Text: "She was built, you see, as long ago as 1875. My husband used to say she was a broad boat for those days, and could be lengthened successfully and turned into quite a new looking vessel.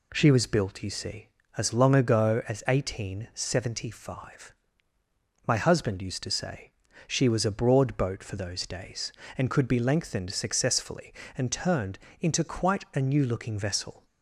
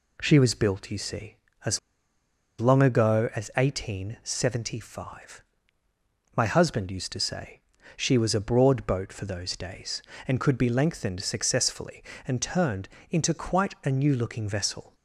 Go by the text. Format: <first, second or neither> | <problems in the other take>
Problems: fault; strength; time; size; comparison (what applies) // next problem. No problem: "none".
first | pauses between "as" and "long"; noticeable; at 1.7 s; 0.79 s long // pauses between "say" and "she"; slight; at 7.6 s; 0.34 s long; slight in the first // pauses between "turned" and "into"; slight; at 12.8 s; 0.22 s long; slight in the first